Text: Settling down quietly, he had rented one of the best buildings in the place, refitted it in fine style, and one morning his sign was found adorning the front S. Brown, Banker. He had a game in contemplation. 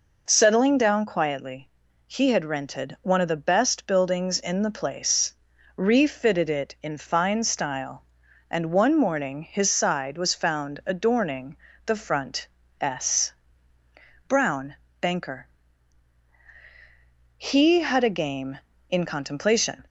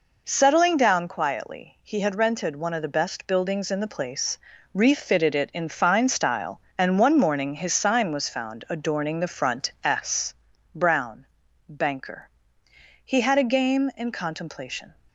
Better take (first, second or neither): second